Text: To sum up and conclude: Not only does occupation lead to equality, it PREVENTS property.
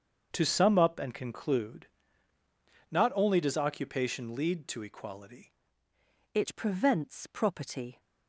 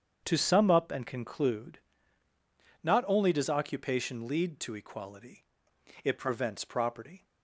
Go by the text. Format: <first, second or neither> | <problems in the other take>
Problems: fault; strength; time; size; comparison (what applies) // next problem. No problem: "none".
second | starts louder than the rest; until 1.3 s; 7 dB; strong in the second // changes voice at "it"; from 6.3 s on; 1.6 s long